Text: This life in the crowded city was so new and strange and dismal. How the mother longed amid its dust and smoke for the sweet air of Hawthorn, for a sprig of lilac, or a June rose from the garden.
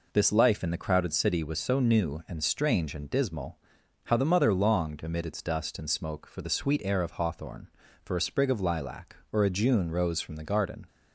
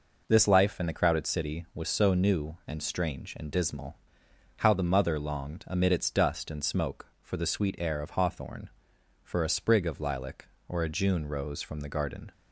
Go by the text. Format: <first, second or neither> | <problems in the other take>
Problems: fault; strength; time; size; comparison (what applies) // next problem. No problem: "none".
neither | none